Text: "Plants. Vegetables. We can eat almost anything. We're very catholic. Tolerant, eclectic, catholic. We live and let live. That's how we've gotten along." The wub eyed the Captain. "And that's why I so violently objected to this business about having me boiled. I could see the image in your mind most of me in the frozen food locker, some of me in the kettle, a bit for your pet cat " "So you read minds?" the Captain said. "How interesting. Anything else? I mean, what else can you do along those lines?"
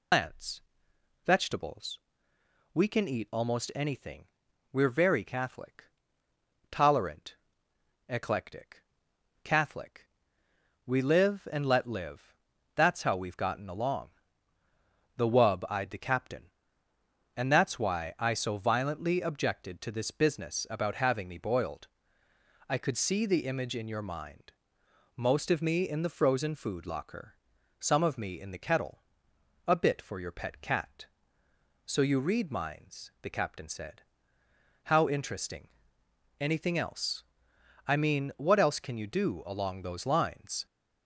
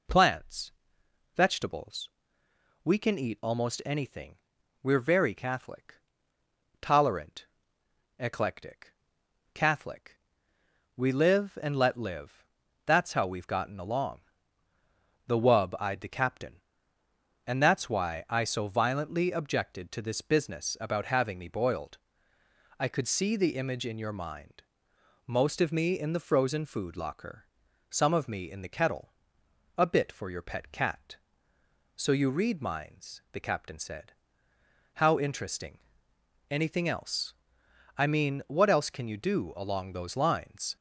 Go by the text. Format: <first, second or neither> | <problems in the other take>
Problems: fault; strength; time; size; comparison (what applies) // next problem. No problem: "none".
second | loses the start of "Plants"; at 0.1 s; 145 ms // pauses between "mind" and "most"; noticeable; at 24.5 s; 0.64 s long; noticeable in the second